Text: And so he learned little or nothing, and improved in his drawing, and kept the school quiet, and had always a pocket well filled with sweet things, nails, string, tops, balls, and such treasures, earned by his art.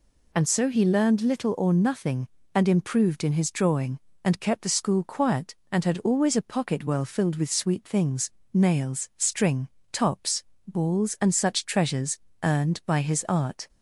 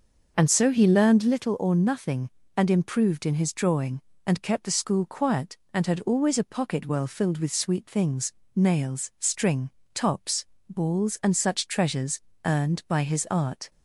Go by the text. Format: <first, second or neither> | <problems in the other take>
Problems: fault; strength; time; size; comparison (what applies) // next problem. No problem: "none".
first | starts louder than the rest; until 1.4 s; 6 dB